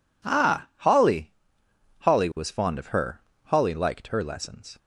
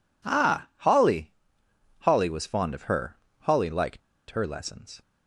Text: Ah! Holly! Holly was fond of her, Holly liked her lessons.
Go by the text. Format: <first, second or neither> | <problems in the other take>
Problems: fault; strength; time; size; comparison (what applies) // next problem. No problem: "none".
first | pauses between "liked" and "her"; slight; at 4.0 s; 0.30 s long